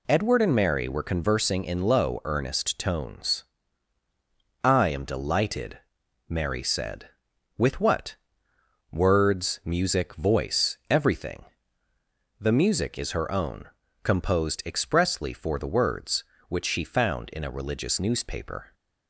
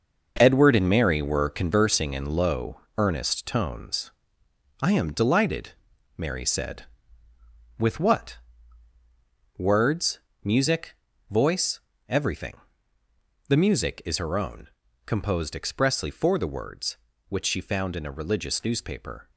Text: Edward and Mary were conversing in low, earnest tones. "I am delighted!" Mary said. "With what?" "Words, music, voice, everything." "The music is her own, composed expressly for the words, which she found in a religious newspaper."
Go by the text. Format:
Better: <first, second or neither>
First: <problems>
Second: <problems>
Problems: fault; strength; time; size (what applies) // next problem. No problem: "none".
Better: first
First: none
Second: gets quieter; strong; throughout; 8.5 dB